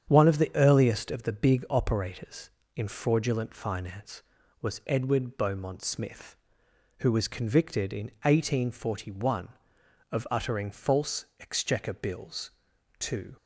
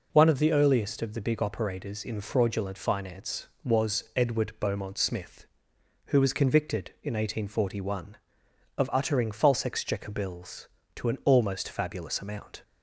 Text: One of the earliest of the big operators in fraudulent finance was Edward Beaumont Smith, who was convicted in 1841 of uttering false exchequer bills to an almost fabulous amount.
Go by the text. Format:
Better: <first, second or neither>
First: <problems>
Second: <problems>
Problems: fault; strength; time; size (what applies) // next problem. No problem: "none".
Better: second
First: starts louder than the rest; strong; until 1.1 s; 8.5 dB // stops before "an almost fabulous amount"; at 13.3 s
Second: none